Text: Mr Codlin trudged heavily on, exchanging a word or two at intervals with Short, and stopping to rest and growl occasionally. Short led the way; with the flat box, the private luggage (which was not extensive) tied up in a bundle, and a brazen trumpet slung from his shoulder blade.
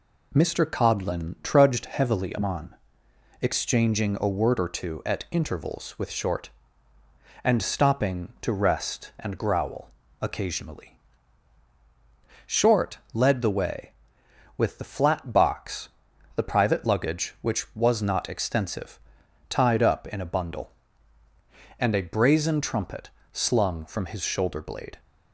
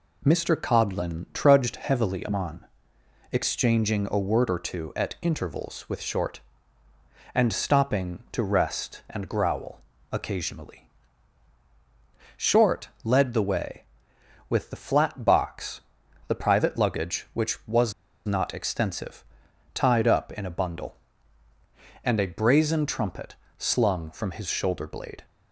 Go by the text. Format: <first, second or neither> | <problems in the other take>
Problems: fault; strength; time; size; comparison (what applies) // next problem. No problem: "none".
first | pauses between "growl" and "occasionally"; slight; at 9.8 s; 0.32 s long; slight in the first // pauses between "Short" and "led"; slight; at 12.8 s; 0.16 s long; slight in the first // pauses between "was" and "not"; slight; at 17.9 s; 0.33 s long // pauses between "trumpet" and "slung"; slight; at 23.3 s; 0.24 s long; slight in the first